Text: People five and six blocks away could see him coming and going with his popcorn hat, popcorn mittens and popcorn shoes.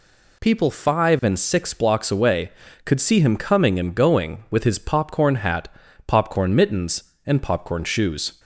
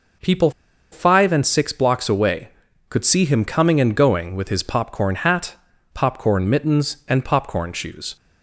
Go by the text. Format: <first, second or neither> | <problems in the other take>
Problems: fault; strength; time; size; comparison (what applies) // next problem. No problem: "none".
first | pauses between "People" and "five"; at 0.5 s; 0.41 s long